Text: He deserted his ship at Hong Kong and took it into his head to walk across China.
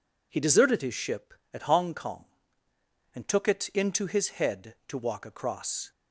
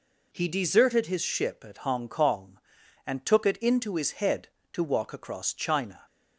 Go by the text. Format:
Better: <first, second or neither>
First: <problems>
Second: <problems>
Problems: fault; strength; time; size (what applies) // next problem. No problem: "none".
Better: second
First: stops before "China"; at 5.9 s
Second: none